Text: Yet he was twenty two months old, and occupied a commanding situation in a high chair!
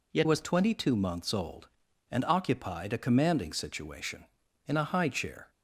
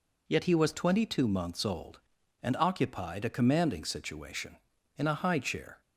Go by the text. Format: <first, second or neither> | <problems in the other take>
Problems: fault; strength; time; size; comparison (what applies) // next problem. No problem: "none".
second | skips "he"; at 0.2 s